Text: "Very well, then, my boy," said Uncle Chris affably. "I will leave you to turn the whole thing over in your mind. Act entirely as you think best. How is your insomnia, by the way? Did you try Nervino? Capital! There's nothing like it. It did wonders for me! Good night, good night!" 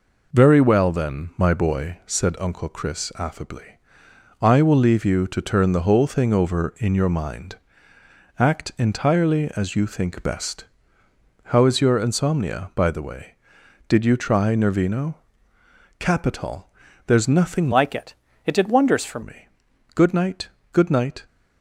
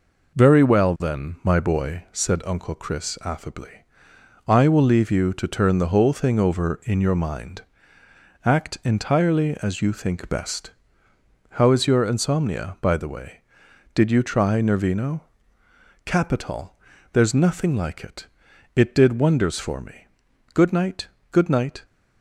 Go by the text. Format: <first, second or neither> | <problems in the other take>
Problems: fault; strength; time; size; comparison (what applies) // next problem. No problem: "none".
second | changes voice from "like" to "for"; from 17.7 to 19.2 s; 1.5 s long